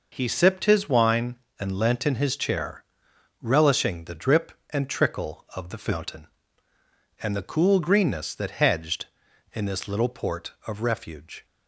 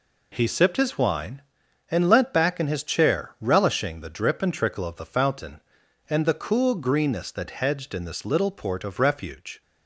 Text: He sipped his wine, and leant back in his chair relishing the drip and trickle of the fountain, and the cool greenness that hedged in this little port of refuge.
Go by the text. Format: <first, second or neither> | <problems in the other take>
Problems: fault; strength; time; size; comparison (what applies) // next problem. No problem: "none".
second | skips "back"; at 2.0 s // pauses between "chair" and "relishing"; noticeable; at 2.8 s; 0.58 s long